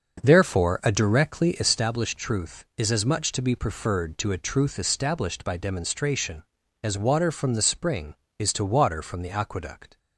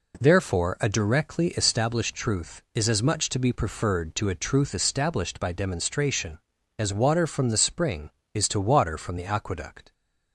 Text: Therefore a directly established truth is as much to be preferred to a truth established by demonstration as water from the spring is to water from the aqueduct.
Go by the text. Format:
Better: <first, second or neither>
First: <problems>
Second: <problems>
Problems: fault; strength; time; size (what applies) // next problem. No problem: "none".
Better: second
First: starts louder than the rest; until 1.8 s; 6.5 dB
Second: none